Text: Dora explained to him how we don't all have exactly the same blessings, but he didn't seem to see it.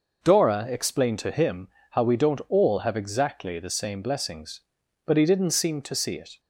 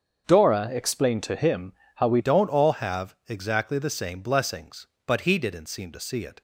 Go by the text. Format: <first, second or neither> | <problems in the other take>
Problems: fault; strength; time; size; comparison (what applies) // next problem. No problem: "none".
first | starts louder than the rest; until 1.2 s; 7 dB // pauses between "him" and "how"; slight; at 1.7 s; 0.24 s long; slight in the first // changes voice at "don't"; from 2.1 s on; 4.3 s long